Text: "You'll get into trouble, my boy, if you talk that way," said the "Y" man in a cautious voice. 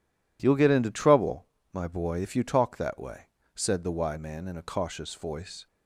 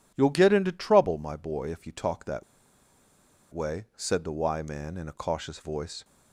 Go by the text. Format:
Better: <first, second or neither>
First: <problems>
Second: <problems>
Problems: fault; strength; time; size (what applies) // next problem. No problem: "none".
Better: first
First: none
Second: pauses between "that" and "way"; at 2.4 s; 1.0 s long